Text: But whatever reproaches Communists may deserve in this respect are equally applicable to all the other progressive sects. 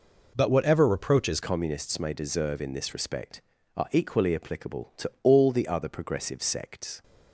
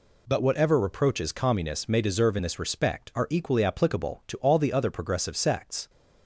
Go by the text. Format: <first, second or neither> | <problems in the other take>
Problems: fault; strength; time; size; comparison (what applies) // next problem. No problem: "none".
second | changes voice at "Communists"; from 1.4 s on; 5.6 s long